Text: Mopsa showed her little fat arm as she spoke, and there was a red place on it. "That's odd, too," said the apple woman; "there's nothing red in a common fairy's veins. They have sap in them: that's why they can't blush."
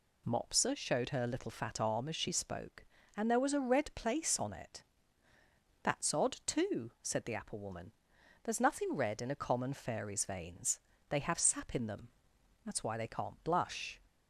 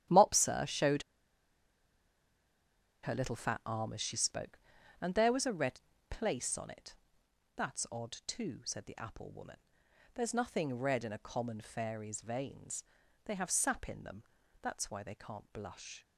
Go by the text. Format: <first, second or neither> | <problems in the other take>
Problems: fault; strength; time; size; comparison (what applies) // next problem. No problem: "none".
first | starts louder than the rest; strong; until 3.1 s; 11.5 dB // pauses between "showed" and "her"; strong; at 1.0 s; 2.0 s long // pauses between "red" and "place"; slight; at 5.7 s; 0.30 s long